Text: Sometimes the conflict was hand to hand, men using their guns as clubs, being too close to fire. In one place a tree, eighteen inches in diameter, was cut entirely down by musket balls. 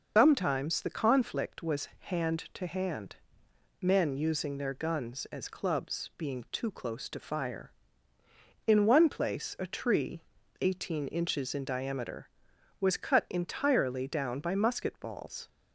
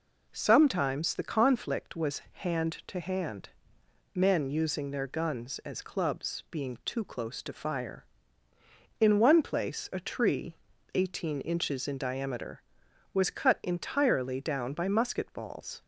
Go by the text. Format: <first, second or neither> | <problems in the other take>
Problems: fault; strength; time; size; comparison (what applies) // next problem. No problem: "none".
second | loses the start of "Sometimes"; at 0.1 s; 190 ms